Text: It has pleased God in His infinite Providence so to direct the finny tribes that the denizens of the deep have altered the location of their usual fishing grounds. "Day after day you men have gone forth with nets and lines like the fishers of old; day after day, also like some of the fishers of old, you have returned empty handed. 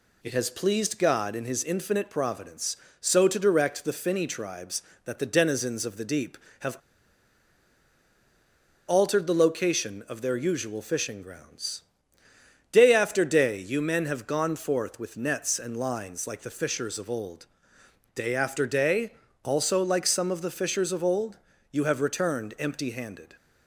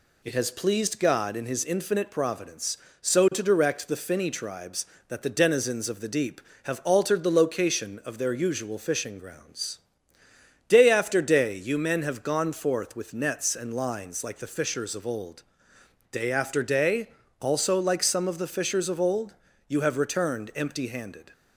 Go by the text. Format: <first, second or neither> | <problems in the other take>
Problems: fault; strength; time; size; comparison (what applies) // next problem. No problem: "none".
second | pauses between "have" and "altered"; strong; at 6.7 s; 2.1 s long